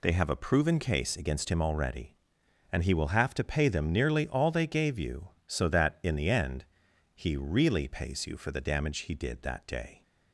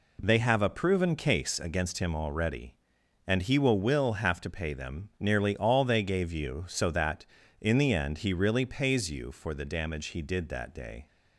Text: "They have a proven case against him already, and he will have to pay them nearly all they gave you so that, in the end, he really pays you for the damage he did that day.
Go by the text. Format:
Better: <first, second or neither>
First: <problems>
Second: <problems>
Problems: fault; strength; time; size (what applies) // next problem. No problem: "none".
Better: first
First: none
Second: says "will" twice; at 3.8 s